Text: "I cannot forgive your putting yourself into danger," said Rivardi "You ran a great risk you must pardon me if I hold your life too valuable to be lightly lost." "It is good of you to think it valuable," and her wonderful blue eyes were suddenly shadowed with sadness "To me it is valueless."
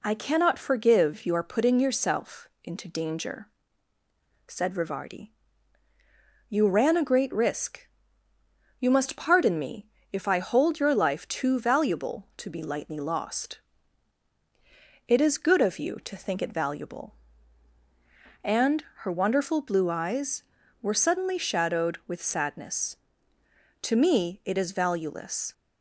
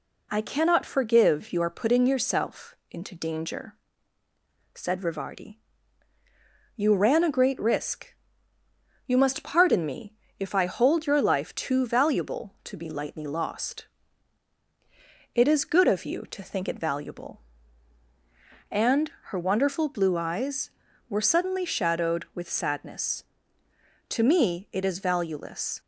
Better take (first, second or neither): neither